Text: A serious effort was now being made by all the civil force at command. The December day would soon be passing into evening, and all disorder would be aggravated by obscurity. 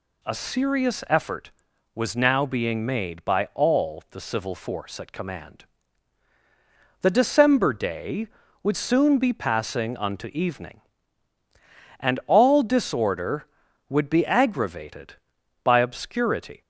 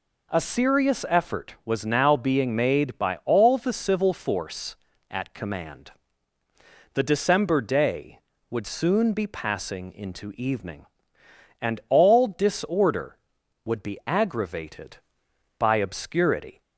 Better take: second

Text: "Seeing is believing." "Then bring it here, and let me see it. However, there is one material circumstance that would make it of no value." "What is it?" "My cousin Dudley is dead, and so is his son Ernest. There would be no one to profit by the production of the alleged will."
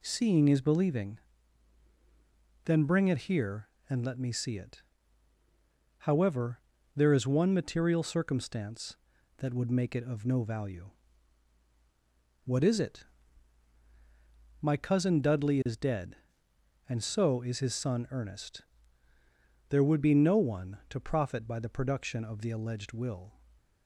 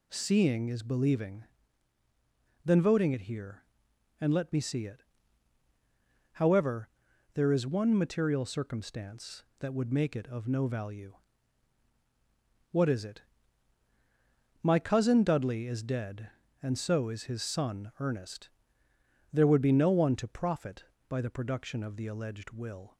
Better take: first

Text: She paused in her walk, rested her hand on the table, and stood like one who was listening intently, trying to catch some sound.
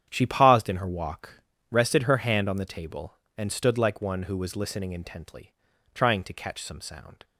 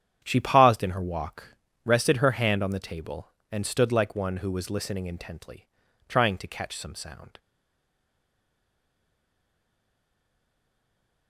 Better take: first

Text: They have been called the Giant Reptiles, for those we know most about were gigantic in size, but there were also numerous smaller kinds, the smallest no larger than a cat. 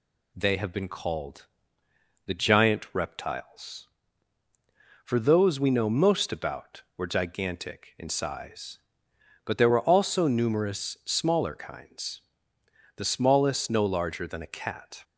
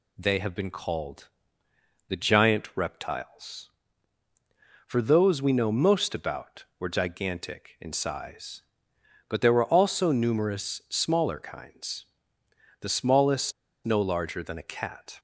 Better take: first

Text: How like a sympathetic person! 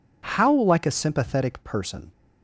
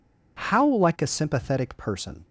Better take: neither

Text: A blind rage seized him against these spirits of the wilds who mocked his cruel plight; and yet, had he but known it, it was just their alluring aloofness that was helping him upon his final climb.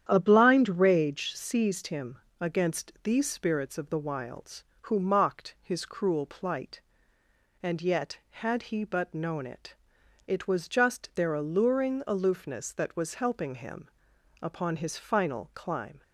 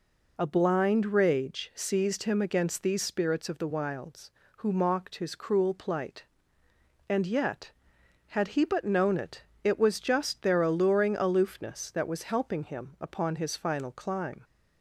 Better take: second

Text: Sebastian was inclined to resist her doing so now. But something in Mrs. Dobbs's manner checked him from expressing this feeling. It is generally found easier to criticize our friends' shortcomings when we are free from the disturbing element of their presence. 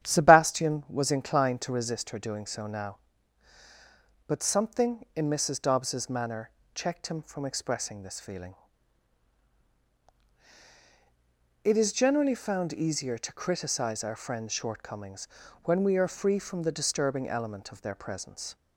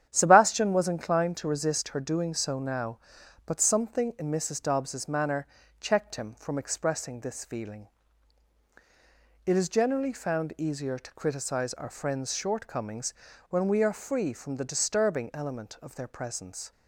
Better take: neither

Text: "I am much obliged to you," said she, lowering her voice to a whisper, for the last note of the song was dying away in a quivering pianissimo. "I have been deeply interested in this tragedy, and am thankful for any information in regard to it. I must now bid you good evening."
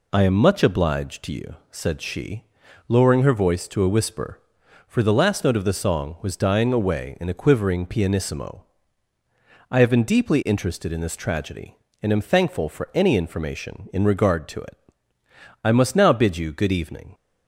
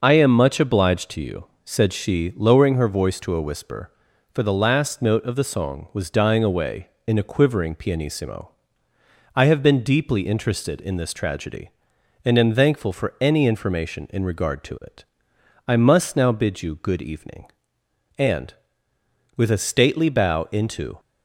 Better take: first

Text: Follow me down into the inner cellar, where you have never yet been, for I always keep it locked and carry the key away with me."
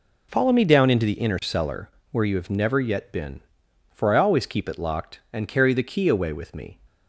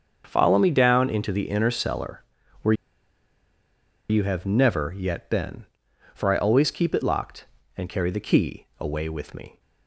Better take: first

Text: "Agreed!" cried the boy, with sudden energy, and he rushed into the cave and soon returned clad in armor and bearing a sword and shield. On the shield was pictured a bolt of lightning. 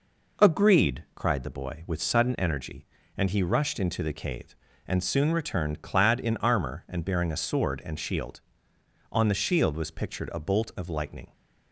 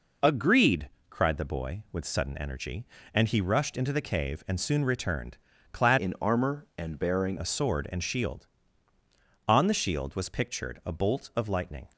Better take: first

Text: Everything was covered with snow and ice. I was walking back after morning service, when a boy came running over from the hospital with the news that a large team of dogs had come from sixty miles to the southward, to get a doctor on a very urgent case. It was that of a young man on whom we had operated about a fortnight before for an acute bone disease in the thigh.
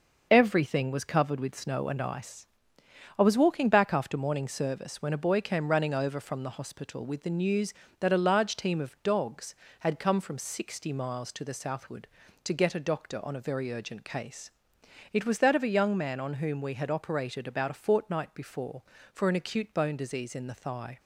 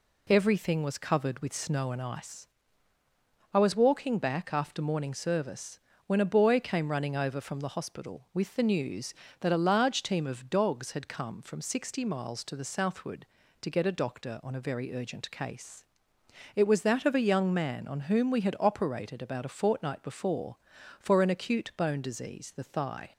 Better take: first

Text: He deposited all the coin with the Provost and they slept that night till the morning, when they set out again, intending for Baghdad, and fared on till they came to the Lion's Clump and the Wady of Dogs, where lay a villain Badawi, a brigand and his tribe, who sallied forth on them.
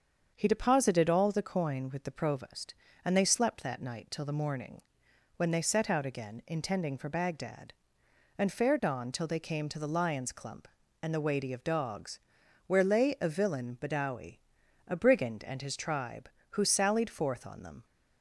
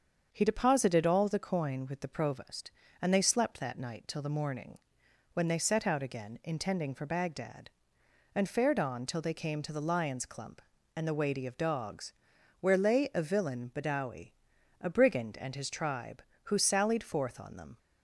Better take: neither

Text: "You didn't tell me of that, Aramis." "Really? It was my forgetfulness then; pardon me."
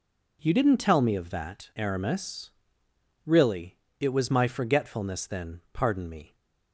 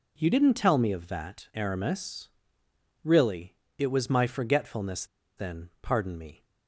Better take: first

